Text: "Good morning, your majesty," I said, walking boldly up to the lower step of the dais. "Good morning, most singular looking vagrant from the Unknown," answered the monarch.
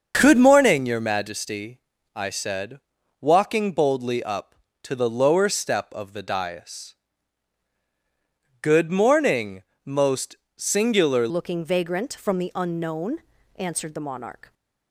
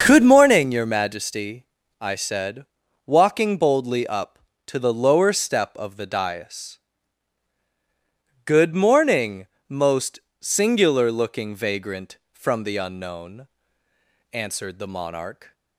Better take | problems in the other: second | starts louder than the rest; until 1.2 s; 6.5 dB; also in the second // pauses between "most" and "singular"; slight; at 10.3 s; 0.20 s long; slight in the second // changes voice at "looking"; from 11.2 s on; 3.3 s long

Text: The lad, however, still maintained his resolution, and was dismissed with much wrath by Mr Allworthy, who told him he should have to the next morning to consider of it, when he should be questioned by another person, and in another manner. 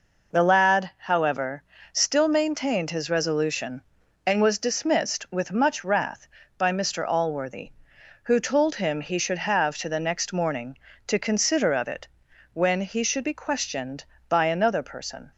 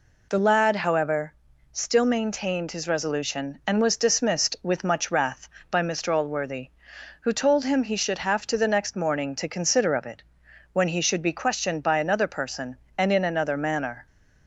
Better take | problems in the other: second | stops before "and in another manner"; at 15.3 s

